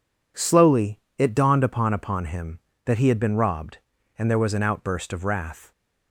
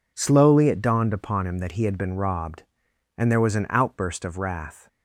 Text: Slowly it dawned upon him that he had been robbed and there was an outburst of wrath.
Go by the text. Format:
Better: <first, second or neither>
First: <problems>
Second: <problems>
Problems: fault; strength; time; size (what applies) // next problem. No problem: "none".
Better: second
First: pauses between "Slowly" and "it"; slight; at 0.9 s; 0.18 s long // says "upon" twice; at 1.9 s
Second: none